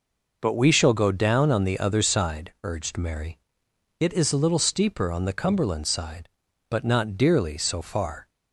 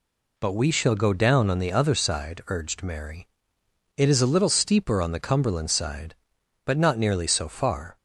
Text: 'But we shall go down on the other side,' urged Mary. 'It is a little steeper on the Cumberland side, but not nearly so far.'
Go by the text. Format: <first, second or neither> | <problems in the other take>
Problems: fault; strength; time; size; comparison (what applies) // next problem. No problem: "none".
second | says "dearly" for "nearly"; at 7.1 s